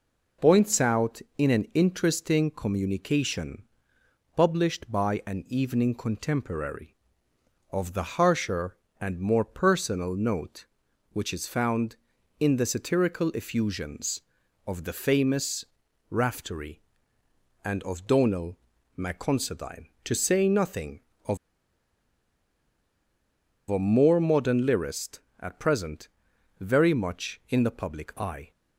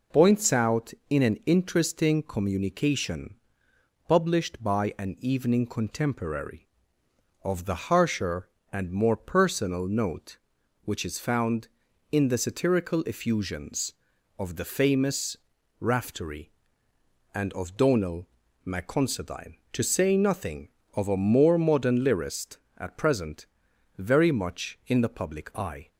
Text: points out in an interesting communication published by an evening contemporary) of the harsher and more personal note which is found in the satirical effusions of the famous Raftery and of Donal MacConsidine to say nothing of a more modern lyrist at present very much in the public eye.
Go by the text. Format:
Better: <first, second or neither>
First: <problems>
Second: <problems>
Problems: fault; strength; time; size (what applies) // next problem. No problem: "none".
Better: second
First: pauses between "communication" and "published"; noticeable; at 3.6 s; 0.74 s long // pauses between "famous" and "Raftery"; noticeable; at 15.6 s; 0.46 s long // pauses between "Donal" and "MacConsidine"; at 18.5 s; 0.40 s long // pauses between "of" and "a"; strong; at 21.3 s; 2.3 s long // pauses between "present" and "very"; noticeable; at 26.0 s; 0.52 s long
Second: pauses between "communication" and "published"; noticeable; at 3.3 s; 0.74 s long // pauses between "famous" and "Raftery"; at 15.3 s; 0.44 s long // pauses between "Donal" and "MacConsidine"; at 18.2 s; 0.38 s long // pauses between "present" and "very"; noticeable; at 23.4 s; 0.52 s long